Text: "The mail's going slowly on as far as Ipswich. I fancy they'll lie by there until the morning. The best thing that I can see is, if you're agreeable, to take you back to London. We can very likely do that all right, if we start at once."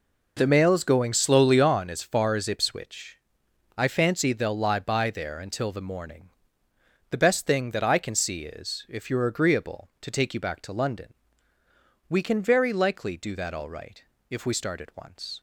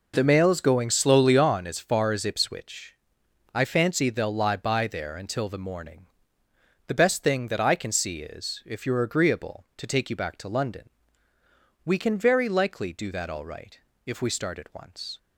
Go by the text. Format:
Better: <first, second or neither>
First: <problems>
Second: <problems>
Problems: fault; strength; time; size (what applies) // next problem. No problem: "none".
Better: neither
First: none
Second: none